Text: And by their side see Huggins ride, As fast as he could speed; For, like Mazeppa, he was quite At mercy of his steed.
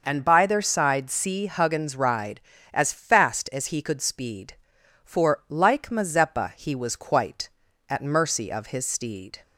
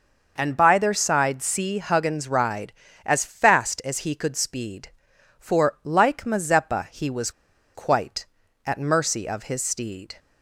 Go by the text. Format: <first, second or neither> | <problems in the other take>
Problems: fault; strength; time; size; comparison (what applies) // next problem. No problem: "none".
first | pauses between "was" and "quite"; at 7.3 s; 0.44 s long